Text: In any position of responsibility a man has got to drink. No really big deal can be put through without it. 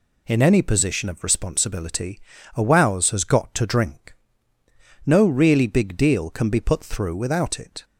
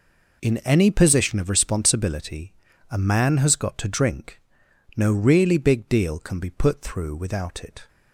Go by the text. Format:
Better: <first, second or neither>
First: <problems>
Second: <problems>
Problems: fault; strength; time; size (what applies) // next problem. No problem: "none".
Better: second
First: pauses between "responsibility" and "a"; slight; at 2.2 s; 0.34 s long // says "wows" for "man"; at 2.6 s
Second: pauses between "responsibility" and "a"; at 2.5 s; 0.38 s long